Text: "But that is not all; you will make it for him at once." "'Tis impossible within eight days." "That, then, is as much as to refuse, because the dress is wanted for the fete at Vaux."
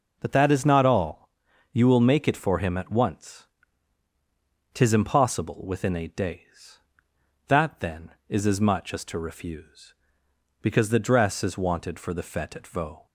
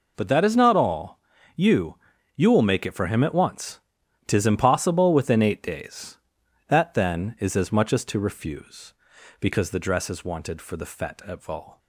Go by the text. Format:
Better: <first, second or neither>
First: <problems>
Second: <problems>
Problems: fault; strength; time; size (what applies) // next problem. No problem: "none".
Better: first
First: none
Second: says "you" twice; at 2.3 s